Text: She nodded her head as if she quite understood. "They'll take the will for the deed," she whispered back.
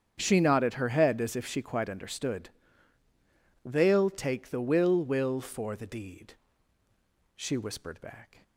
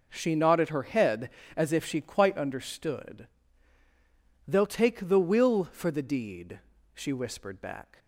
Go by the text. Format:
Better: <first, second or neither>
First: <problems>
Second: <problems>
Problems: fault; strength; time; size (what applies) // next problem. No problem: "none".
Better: second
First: starts louder than the rest; strong; until 1.1 s; 8 dB // says "will" twice; at 5.0 s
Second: none